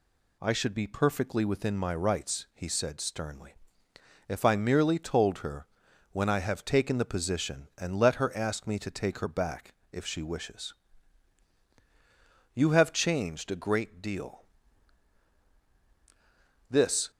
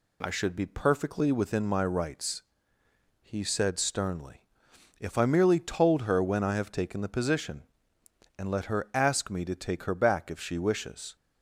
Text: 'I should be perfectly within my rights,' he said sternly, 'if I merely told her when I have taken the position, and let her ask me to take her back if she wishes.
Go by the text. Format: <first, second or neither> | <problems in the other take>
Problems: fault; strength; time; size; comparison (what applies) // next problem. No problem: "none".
second | pauses between "her" and "when"; noticeable; at 5.6 s; 0.46 s long // pauses between "back" and "if"; slight; at 9.7 s; 0.18 s long // goes on to say "You have changed a great deal this"; strong; from 12.5 s on; 4.5 s long